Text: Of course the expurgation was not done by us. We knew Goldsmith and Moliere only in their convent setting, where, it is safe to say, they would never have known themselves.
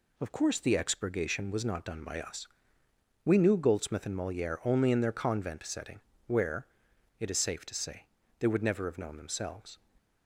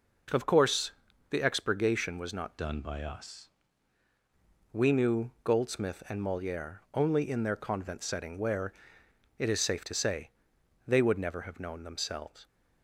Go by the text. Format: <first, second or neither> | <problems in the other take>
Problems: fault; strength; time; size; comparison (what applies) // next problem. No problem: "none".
first | pauses between "course" and "the"; at 0.9 s; 0.40 s long // changes voice from "done" to "us"; from 2.5 to 3.4 s; 0.9 s long